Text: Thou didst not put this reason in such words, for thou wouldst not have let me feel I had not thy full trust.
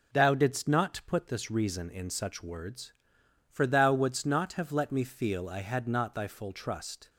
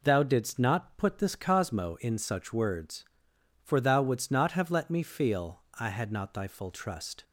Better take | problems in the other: first | says "cosmo" for "reason"; at 1.3 s // pauses between "feel" and "I"; slight; at 5.6 s; 0.18 s long

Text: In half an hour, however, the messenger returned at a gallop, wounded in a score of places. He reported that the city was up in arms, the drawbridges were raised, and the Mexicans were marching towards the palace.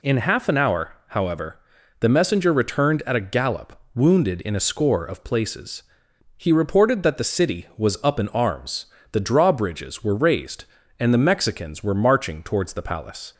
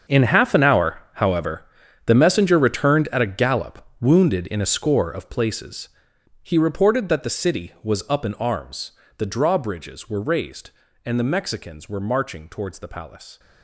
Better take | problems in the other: first | gets quieter; strong; throughout; 15.5 dB

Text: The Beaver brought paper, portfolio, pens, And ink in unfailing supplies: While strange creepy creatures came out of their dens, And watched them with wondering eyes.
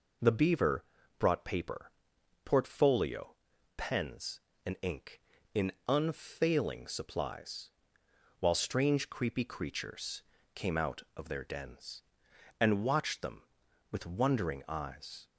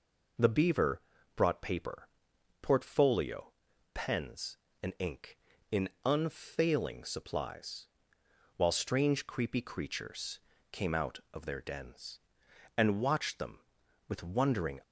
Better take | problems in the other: first | pauses between "Beaver" and "brought"; slight; at 0.9 s; 0.36 s long; slight in the first // pauses between "in" and "unfailing"; slight; at 5.8 s; 0.18 s long; slight in the first // pauses between "creatures" and "came"; slight; at 10.4 s; 0.32 s long; slight in the first // stops before "eyes"; at 14.8 s

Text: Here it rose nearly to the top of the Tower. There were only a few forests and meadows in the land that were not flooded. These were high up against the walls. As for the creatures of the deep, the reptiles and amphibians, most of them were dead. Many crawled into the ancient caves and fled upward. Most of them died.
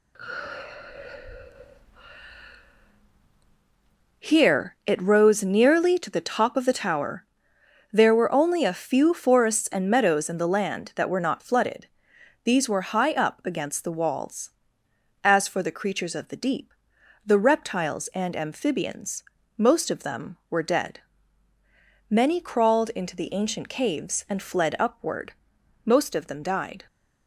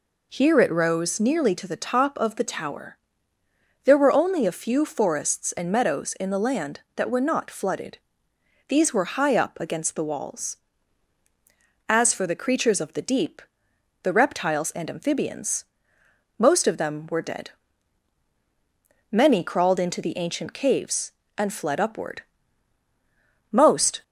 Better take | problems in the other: first | stops before "of them died"; at 24.0 s

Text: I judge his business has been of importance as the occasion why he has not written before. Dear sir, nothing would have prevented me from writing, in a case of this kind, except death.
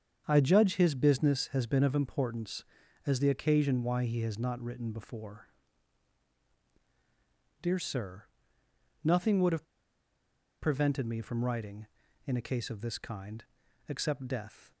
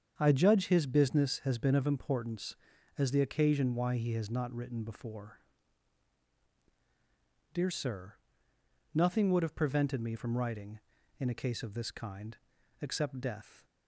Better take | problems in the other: second | starts louder than the rest; strong; until 1.2 s; 7.5 dB; strong in the second // pauses between "have" and "prevented"; noticeable; at 9.6 s; 0.96 s long

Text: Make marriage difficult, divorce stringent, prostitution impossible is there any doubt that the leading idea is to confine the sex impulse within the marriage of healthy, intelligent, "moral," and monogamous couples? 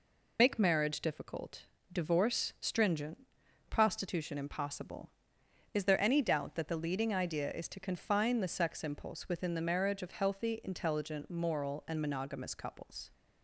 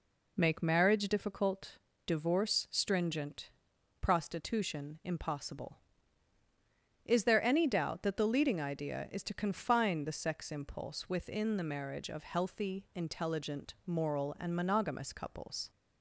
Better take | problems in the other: second | loses the start of "Make"; at 0.3 s; 55 ms

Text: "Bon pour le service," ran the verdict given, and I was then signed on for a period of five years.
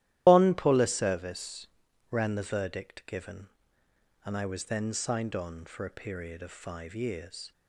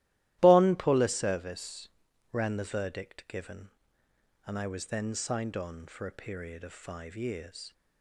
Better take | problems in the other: second | loses the start of "Bon"; at 0.2 s; 75 ms // starts louder than the rest; strong; until 1.2 s; 14 dB; strong in the second

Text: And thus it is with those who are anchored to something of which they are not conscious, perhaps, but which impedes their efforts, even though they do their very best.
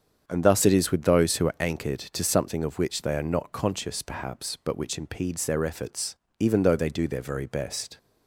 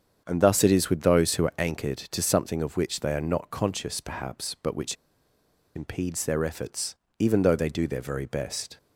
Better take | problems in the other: first | starts louder than the rest; strong; until 1.2 s; 7.5 dB; strong in the first // pauses between "which" and "impedes"; noticeable; at 4.9 s; 0.80 s long

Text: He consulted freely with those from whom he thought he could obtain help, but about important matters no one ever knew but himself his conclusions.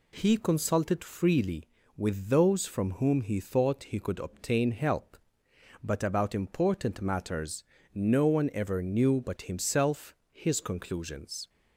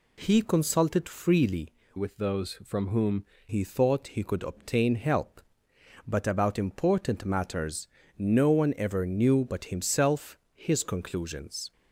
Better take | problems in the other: first | changes voice from "with" to "whom"; from 1.9 to 3.2 s; 1.3 s long // pauses between "matters" and "no"; slight; at 7.8 s; 0.32 s long; slight in the first // pauses between "himself" and "his"; slight; at 10.3 s; 0.16 s long; slight in the first

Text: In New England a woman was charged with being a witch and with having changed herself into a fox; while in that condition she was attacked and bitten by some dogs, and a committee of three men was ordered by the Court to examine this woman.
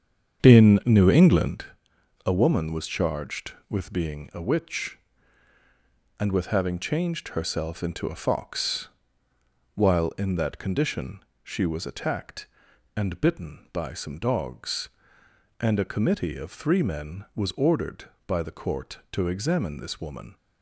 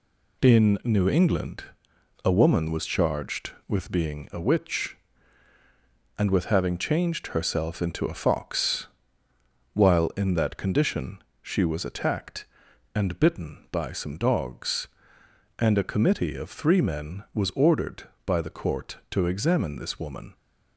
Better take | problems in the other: second | starts louder than the rest; strong; until 1.6 s; 8 dB // pauses between "England" and "a"; noticeable; at 1.6 s; 0.58 s long; noticeable in the second // pauses between "condition" and "she"; slight; at 11.2 s; 0.22 s long; slight in the second

